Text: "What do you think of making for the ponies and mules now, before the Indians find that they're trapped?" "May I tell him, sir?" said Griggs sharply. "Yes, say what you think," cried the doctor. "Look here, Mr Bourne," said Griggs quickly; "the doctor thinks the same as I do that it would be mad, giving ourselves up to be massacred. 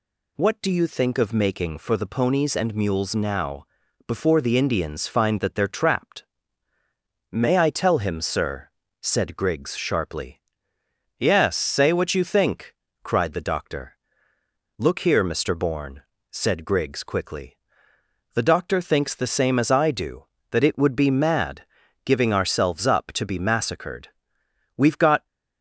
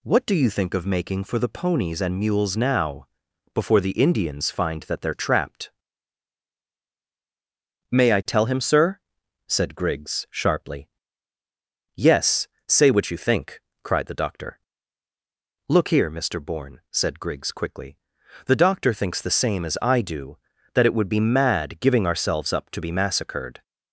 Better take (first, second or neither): second